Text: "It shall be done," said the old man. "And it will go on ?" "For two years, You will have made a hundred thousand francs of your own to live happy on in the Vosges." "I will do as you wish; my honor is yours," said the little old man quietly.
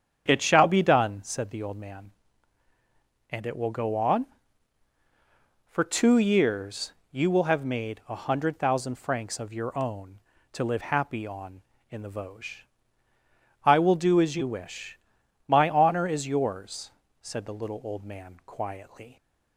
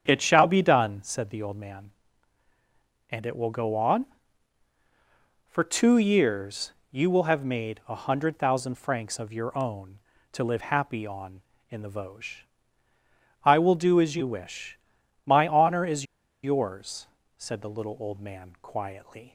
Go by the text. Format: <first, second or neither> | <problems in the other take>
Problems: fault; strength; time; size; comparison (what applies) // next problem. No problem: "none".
first | starts louder than the rest; strong; until 1.0 s; 8 dB; strong in the first // pauses between "is" and "yours"; at 16.0 s; 0.38 s long